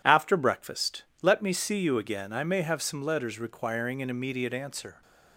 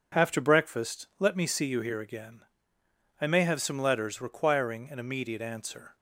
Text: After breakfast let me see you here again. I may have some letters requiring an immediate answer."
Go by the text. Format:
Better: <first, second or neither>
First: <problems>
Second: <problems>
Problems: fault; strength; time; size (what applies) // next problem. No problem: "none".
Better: second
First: pauses between "breakfast" and "let"; slight; at 1.0 s; 0.18 s long // skips "here"; at 1.9 s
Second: none